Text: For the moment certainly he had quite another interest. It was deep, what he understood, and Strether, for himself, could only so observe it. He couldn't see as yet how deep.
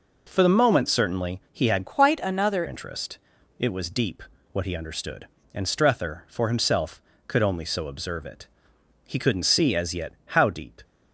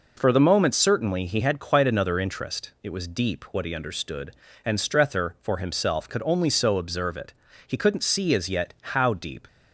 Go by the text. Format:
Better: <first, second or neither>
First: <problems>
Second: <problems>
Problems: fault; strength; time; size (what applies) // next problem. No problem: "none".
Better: second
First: changes voice from "quite" to "another"; from 1.8 to 2.6 s; 0.8 s long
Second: none